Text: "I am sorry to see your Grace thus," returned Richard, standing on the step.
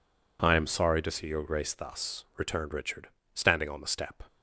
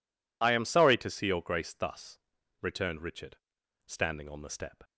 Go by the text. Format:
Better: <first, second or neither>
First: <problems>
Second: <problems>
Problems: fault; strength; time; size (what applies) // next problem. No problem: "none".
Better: neither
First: none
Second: none